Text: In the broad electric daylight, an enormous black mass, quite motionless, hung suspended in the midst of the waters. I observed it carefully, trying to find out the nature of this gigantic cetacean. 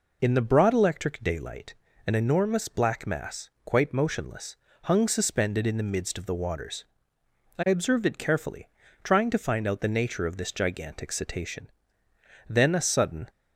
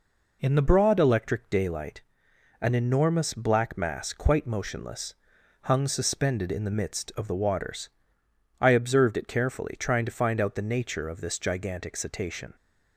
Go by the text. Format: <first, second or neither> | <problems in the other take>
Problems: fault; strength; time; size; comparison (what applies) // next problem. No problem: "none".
second | goes on to say "Then a sudden"; noticeable; from 12.4 s on; 0.80 s long